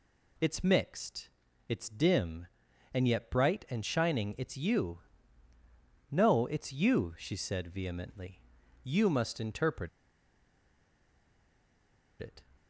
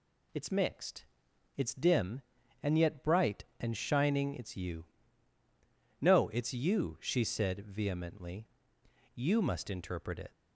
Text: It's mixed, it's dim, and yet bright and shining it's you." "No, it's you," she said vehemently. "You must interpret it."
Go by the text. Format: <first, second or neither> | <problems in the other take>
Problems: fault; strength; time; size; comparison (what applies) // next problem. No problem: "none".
second | pauses between "interpret" and "it"; strong; at 9.8 s; 2.3 s long